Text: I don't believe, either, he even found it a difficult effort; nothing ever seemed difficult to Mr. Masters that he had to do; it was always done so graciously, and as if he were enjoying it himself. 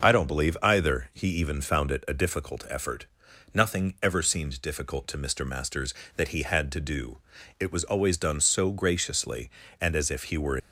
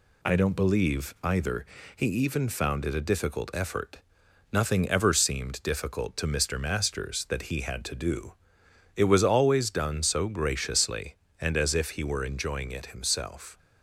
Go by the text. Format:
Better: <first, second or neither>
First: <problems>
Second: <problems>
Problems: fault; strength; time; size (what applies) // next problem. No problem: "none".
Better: second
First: starts louder than the rest; until 1.1 s; 6 dB // stops before "enjoying it himself"; at 10.5 s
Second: none